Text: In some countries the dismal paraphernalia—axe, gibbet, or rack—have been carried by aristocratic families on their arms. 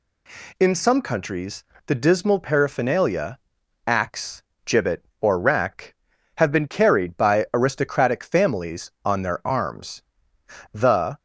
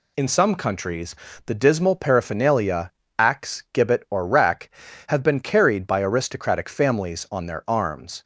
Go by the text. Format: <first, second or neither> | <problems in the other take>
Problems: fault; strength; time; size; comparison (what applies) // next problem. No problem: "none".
second | pauses between "countries" and "the"; slight; at 1.6 s; 0.24 s long; slight in the second // goes on to say "The"; slight; from 10.7 s on; 0.46 s long